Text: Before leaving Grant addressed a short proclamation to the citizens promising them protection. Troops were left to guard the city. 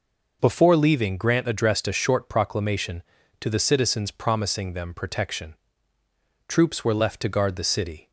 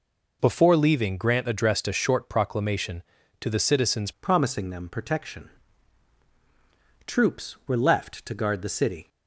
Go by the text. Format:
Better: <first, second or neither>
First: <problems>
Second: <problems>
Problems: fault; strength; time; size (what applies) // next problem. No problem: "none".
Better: first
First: none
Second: changes voice at "promising"; from 4.2 s on; 4.8 s long